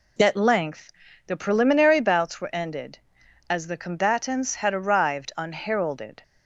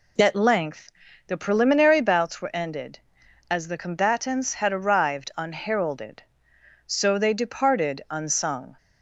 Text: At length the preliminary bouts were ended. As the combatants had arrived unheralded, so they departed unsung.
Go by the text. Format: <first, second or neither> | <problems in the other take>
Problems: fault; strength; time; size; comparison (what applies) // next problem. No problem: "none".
second | pauses between "length" and "the"; slight; at 0.9 s; 0.34 s long; slight in the second // stops before "so they departed unsung"; at 6.2 s